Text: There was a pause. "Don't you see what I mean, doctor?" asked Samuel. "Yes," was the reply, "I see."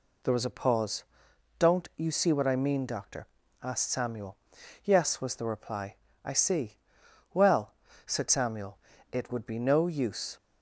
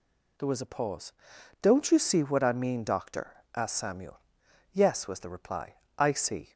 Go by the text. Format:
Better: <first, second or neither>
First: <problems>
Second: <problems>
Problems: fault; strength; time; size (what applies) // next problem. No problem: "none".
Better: second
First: goes on to say "Well said Samuel It would be no use"; strong; from 7.3 s on; 3.0 s long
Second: none